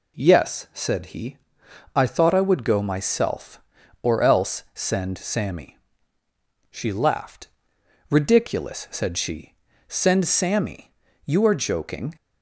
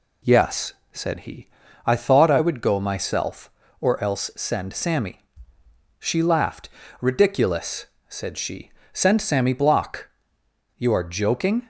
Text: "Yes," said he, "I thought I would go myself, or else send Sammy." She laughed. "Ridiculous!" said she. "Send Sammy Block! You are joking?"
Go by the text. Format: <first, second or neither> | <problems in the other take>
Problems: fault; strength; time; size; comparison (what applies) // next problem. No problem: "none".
second | skips "Block"; at 11.0 s